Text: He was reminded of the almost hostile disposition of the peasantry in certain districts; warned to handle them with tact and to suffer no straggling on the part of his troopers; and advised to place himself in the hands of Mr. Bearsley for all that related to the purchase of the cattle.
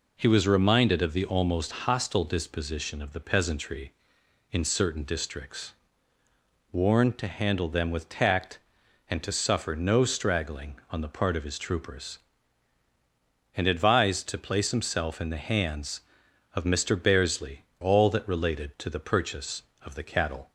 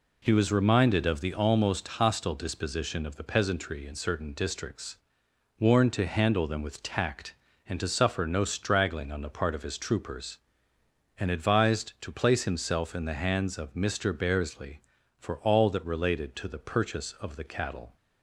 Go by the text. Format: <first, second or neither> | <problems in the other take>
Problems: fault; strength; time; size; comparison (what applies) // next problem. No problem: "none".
second | skips "for"; at 17.7 s